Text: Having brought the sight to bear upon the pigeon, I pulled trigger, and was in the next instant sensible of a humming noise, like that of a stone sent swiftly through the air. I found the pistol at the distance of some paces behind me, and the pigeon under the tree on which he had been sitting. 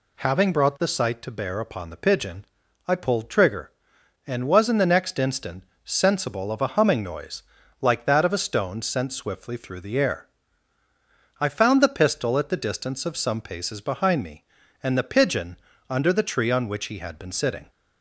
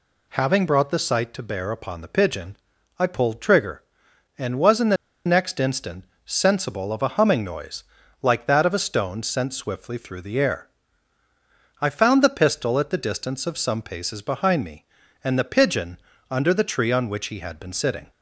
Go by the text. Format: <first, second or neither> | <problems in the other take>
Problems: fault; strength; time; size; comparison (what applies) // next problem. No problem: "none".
first | pauses between "the" and "next"; slight; at 4.9 s; 0.30 s long // pauses between "instant" and "sensible"; slight; at 6.0 s; 0.20 s long; slight in the first // pauses between "pigeon" and "under"; slight; at 15.9 s; 0.32 s long; slight in the first